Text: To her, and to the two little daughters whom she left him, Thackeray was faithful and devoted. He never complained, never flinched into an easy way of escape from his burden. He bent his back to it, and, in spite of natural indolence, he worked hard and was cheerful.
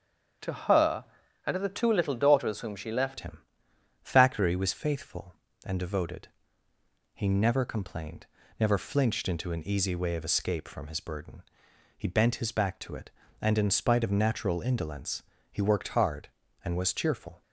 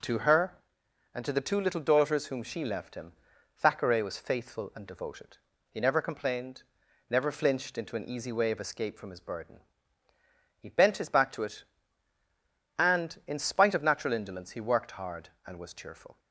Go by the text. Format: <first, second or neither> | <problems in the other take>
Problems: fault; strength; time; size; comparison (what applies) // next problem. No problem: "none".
second | starts louder than the rest; strong; until 1.8 s; 7.5 dB // changes voice at "him"; from 3.2 s on; 14.2 s long